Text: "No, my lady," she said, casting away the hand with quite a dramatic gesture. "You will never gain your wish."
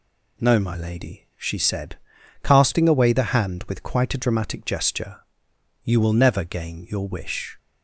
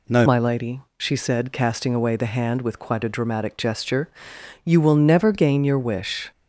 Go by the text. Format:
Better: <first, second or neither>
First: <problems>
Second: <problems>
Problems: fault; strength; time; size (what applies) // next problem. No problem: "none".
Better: first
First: none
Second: changes voice at "my"; from 0.2 s on; 6.1 s long